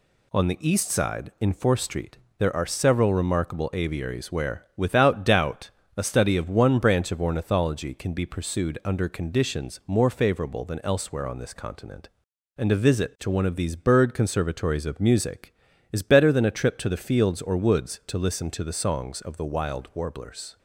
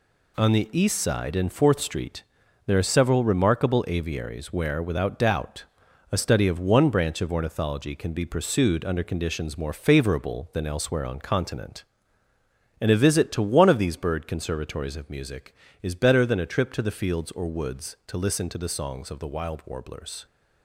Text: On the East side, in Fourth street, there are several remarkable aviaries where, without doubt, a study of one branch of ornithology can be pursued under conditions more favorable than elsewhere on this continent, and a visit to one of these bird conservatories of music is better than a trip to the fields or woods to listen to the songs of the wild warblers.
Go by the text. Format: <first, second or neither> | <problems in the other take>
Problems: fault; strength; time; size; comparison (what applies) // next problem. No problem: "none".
first | skips "this"; at 11.2 s